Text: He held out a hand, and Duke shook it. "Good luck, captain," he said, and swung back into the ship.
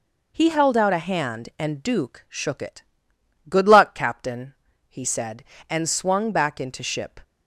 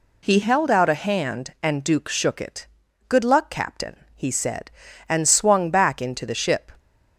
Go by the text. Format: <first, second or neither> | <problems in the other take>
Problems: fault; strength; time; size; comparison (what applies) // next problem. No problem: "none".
second | skips "the"; at 6.8 s